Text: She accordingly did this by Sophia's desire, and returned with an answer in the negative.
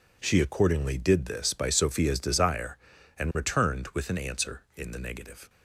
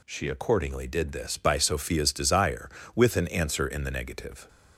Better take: first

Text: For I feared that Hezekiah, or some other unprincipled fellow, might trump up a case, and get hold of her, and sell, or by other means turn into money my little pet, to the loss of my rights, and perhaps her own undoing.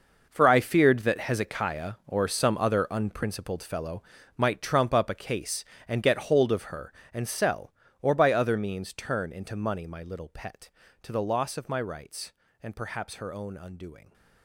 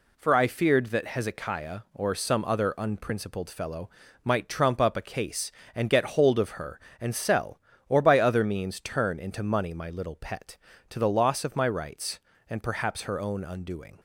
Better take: second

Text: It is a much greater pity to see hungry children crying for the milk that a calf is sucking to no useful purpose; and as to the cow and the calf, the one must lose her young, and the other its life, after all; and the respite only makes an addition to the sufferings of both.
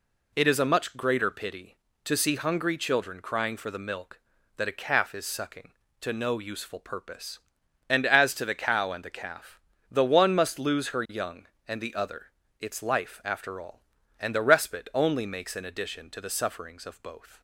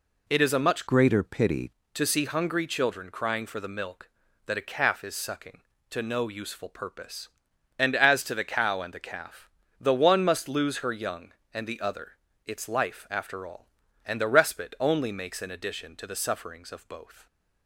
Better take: first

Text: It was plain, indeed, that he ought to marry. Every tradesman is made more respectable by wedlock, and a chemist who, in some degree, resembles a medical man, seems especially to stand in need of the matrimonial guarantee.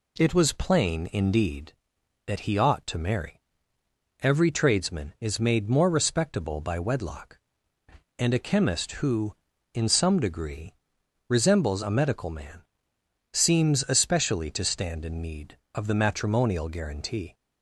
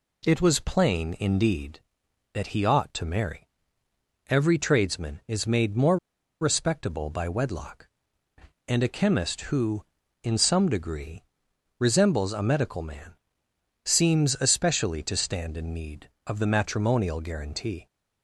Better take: first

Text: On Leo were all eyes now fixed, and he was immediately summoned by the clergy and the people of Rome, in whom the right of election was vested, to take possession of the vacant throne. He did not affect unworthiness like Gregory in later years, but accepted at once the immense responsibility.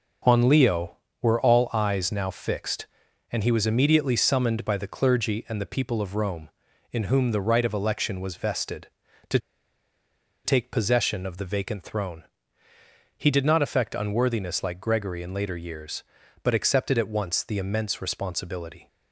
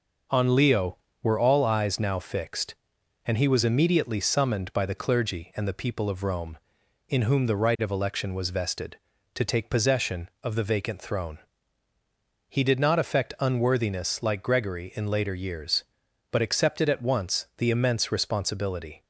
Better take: second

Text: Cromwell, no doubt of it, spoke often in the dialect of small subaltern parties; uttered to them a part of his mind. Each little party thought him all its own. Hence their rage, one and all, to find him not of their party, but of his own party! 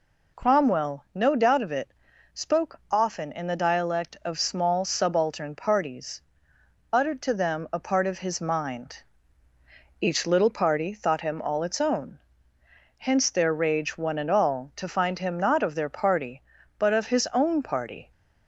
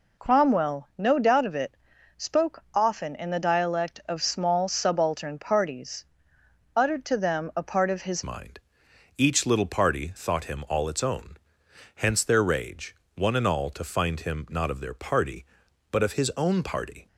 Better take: first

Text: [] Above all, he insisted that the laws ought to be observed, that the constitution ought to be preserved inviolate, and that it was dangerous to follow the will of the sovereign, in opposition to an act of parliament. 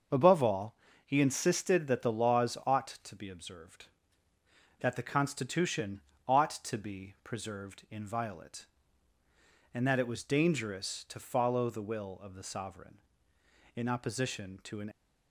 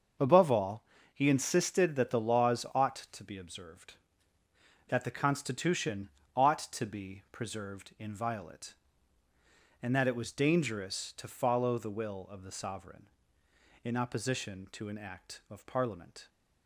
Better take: second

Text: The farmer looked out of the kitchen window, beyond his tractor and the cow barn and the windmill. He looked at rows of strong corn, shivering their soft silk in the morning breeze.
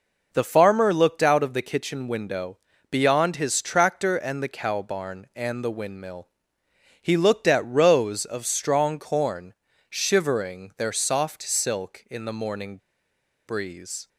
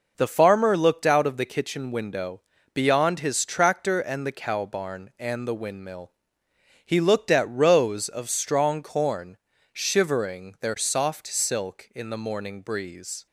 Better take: second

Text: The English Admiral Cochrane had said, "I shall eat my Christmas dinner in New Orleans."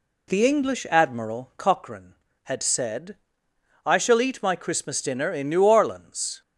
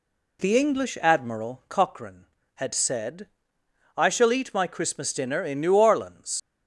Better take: first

